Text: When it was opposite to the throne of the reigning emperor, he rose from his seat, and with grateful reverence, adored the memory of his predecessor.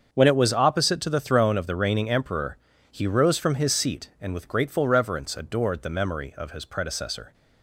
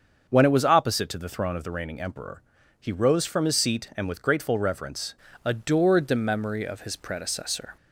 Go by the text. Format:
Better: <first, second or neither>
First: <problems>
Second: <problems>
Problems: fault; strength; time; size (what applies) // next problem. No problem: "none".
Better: first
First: starts louder than the rest; until 1.1 s; 7 dB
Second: starts louder than the rest; until 1.3 s; 6.5 dB // changes voice at "adored"; from 5.4 s on; 2.3 s long